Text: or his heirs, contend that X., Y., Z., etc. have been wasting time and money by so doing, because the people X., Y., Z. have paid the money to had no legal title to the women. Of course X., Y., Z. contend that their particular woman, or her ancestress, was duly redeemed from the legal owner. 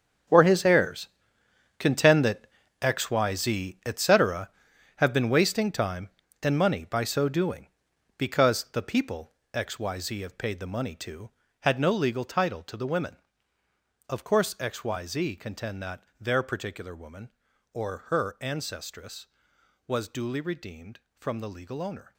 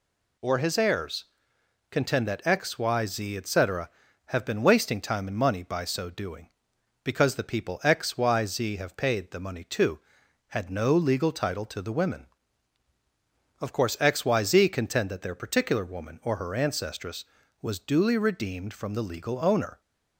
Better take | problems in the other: second | gets quieter; strong; throughout; 13.5 dB // pauses between "that" and "X"; slight; at 2.4 s; 0.34 s long // pauses between "people" and "X"; slight; at 9.3 s; 0.22 s long // pauses between "that" and "their"; slight; at 16.0 s; 0.16 s long

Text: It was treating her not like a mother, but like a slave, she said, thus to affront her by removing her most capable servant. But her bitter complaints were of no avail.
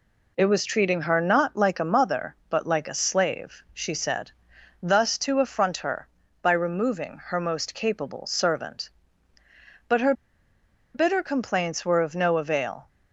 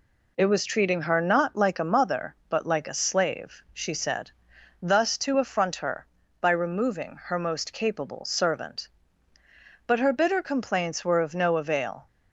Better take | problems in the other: second | pauses between "her" and "bitter"; noticeable; at 10.1 s; 0.82 s long

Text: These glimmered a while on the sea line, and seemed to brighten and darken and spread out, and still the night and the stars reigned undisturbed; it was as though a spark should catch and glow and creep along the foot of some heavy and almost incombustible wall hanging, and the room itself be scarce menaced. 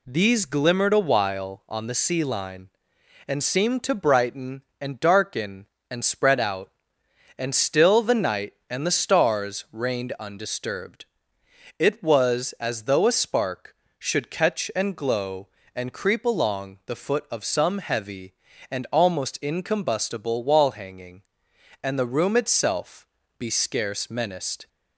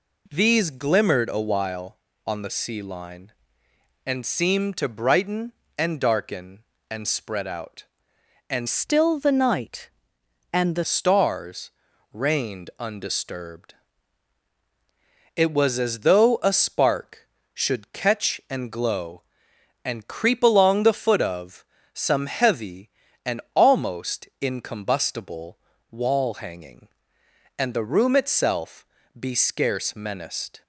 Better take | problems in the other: first | changes voice from "still" to "the"; from 8.6 to 10.8 s; 2.2 s long // pauses between "stars" and "reigned"; at 11.7 s; 0.42 s long // pauses between "of" and "some"; slight; at 21.6 s; 0.30 s long // pauses between "incombustible" and "wall"; slight; at 25.5 s; 0.34 s long // pauses between "itself" and "be"; slight; at 28.8 s; 0.34 s long; slight in the first

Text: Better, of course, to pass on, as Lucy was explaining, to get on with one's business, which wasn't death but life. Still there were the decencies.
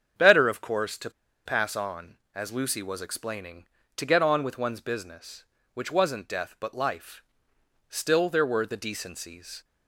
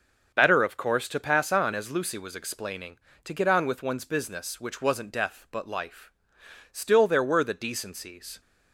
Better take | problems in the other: second | starts louder than the rest; strong; until 1.5 s; 7.5 dB; also in the second // pauses between "to" and "pass"; slight; at 1.1 s; 0.34 s long

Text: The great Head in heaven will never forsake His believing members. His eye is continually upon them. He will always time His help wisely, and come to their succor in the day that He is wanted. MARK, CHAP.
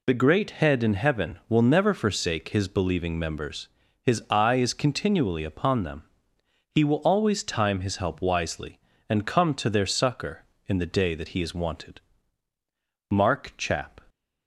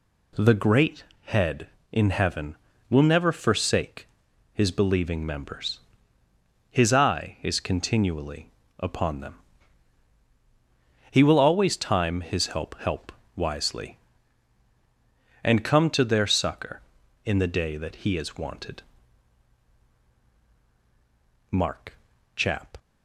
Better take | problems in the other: first | pauses between "great" and "Head"; slight; at 1.0 s; 0.24 s long // pauses between "forsake" and "His"; noticeable; at 4.0 s; 0.46 s long // pauses between "continually" and "upon"; slight; at 8.4 s; 0.28 s long // says "help" twice; at 12.7 s

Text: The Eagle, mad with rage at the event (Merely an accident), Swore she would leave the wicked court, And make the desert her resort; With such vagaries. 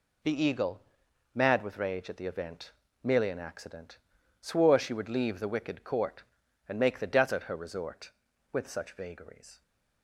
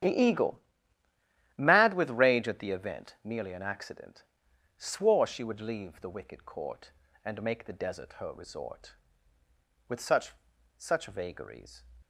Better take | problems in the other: first | starts louder than the rest; strong; until 2.0 s; 10 dB // says "such" twice; at 10.7 s

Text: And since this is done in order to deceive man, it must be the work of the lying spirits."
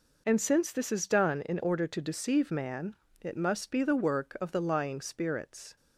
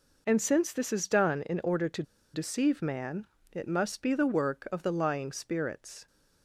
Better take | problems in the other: first | pauses between "to" and "deceive"; slight; at 2.0 s; 0.31 s long

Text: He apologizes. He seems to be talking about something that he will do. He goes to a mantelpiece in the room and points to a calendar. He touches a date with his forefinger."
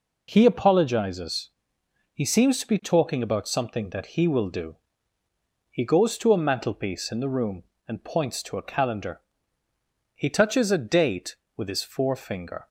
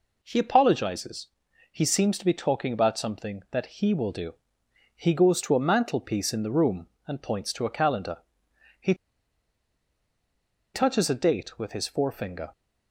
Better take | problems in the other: first | pauses between "He" and "touches"; strong; at 8.9 s; 1.8 s long

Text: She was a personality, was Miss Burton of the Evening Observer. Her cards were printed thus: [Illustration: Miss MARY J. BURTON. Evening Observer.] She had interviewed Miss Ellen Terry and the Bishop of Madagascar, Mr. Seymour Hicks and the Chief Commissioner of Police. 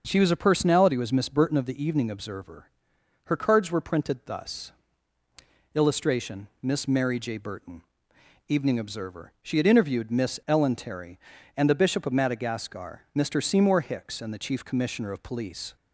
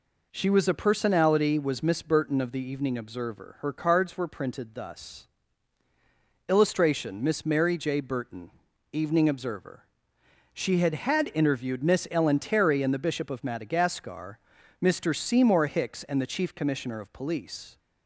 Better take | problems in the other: first | says "had" twice; at 10.9 s

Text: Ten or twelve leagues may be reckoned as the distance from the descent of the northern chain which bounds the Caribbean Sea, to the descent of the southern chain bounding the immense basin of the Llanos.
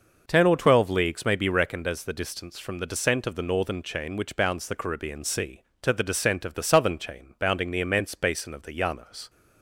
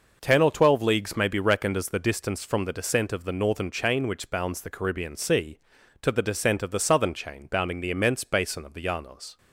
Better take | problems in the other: neither | none

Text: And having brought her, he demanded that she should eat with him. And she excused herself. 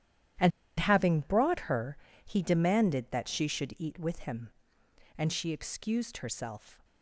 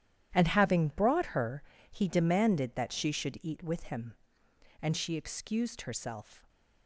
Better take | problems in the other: second | starts louder than the rest; strong; until 1.7 s; 11.5 dB; strong in the second // pauses between "And" and "having"; slight; at 0.5 s; 0.29 s long

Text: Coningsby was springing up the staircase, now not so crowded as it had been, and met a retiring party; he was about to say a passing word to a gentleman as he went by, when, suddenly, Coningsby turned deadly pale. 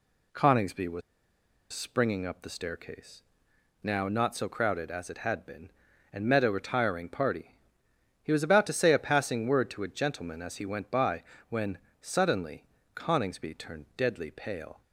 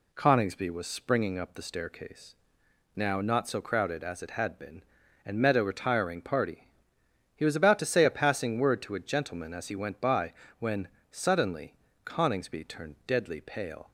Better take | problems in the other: second | pauses between "was" and "springing"; noticeable; at 1.0 s; 0.72 s long

